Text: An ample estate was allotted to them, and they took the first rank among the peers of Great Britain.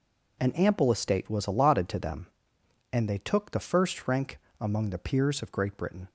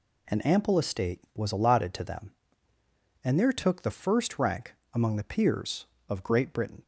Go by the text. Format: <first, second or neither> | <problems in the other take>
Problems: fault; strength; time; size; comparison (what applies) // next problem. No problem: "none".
first | says "there" for "they"; at 3.3 s // pauses between "rank" and "among"; slight; at 4.7 s; 0.18 s long; slight in the first